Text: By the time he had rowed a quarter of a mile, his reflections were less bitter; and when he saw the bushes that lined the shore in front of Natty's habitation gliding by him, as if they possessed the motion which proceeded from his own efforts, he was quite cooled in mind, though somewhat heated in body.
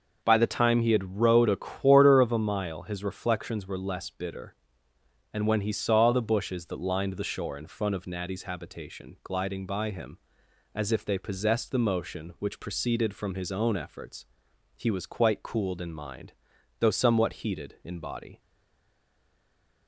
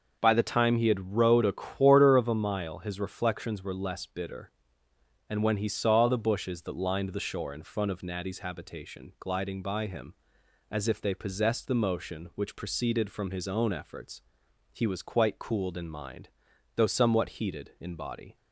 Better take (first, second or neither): second